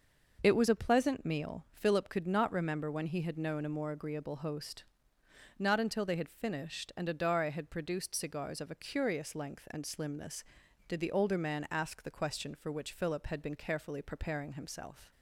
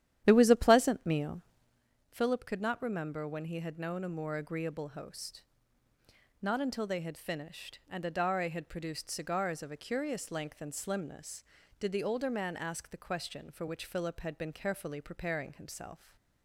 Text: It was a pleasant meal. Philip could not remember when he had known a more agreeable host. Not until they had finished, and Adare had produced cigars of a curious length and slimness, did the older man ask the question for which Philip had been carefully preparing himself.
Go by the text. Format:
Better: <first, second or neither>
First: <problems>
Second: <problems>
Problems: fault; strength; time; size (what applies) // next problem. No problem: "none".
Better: first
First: none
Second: starts louder than the rest; strong; until 1.9 s; 11 dB